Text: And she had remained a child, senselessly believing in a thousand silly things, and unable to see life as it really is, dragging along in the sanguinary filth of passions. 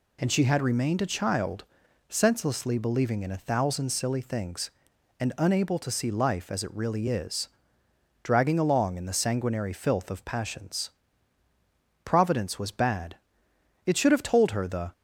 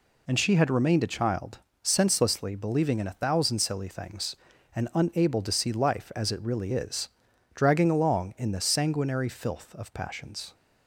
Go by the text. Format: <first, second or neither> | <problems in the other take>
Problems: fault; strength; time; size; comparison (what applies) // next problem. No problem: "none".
second | goes on to say "Providence was bad it should have told her the"; strong; from 12.0 s on; 2.8 s long